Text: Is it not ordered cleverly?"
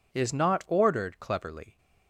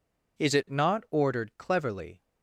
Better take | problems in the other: second | skips "it"; at 0.3 s

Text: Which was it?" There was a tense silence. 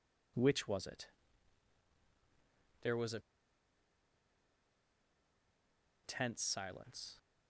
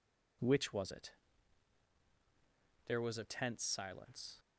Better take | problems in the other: second | pauses between "a" and "tense"; strong; at 3.1 s; 2.8 s long

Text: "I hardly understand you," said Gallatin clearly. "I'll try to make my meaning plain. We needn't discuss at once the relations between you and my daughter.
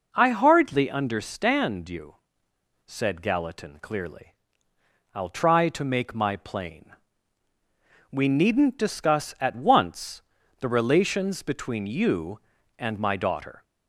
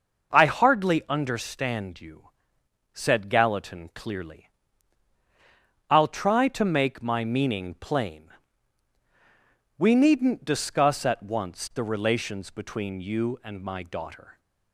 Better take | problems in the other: second | skips "meaning"; at 6.3 s // pauses between "once" and "the"; at 10.2 s; 0.38 s long

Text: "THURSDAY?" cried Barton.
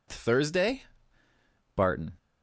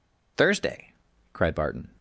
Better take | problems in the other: second | skips "cried"; at 1.2 s

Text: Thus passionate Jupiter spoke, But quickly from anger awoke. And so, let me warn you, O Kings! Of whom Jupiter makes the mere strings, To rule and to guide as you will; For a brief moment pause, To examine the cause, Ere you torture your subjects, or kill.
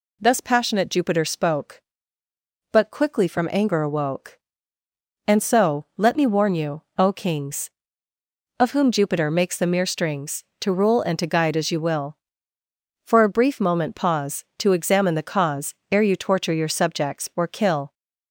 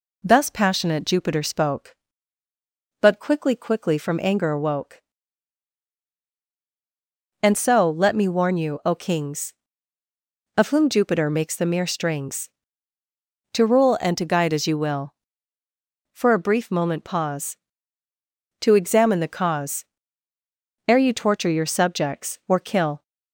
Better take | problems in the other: first | says "quickly" twice; at 3.5 s

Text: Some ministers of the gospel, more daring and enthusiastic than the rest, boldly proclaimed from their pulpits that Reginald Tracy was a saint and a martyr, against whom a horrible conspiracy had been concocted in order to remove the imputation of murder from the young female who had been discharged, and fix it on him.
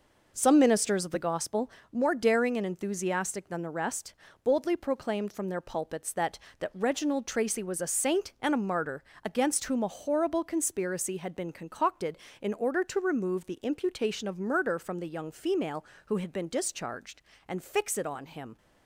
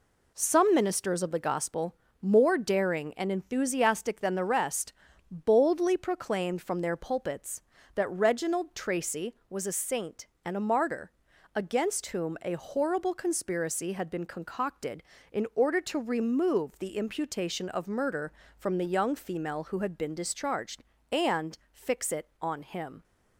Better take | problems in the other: second | says "that" twice; at 6.5 s

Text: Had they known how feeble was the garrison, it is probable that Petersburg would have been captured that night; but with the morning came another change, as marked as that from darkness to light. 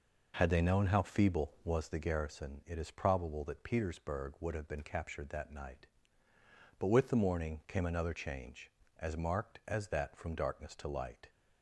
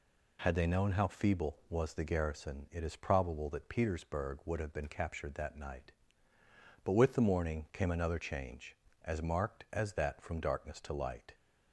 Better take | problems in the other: second | starts louder than the rest; noticeable; until 2.0 s; 5.5 dB

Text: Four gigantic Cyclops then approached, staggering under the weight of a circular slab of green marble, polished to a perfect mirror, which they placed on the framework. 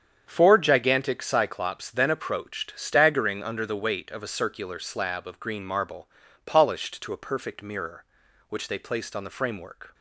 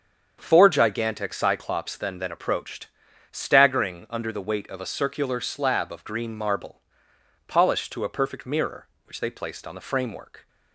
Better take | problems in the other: first | starts louder than the rest; until 1.4 s; 7 dB; strong in the first // says "then" twice; at 2.1 s

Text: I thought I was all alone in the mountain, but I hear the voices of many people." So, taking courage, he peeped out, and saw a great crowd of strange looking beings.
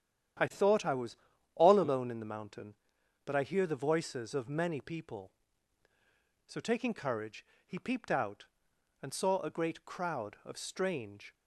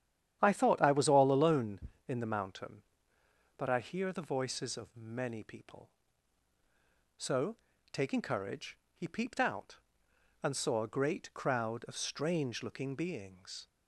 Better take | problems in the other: second | starts louder than the rest; strong; until 1.8 s; 10 dB; strong in the second // pauses between "was" and "all"; at 1.1 s; 0.38 s long // stops before "looking beings"; at 11.3 s

